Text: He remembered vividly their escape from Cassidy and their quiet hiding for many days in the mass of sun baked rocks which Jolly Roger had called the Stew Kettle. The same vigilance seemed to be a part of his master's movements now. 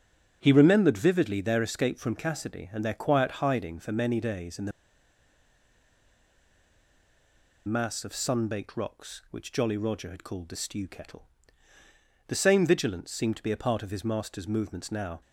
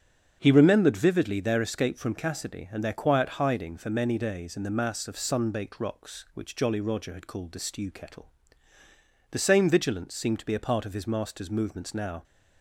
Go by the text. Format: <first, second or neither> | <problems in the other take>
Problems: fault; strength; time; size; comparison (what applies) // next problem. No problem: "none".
second | starts louder than the rest; strong; until 1.4 s; 7.5 dB; strong in the second // pauses between "the" and "mass"; strong; at 4.7 s; 2.9 s long